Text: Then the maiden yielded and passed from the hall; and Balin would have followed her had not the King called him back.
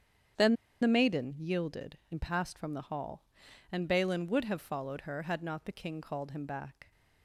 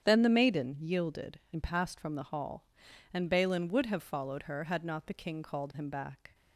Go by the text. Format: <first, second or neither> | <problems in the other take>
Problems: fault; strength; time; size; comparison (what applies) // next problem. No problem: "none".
second | starts louder than the rest; strong; until 1.6 s; 8.5 dB; strong in the second // pauses between "Then" and "the"; slight; at 0.5 s; 0.26 s long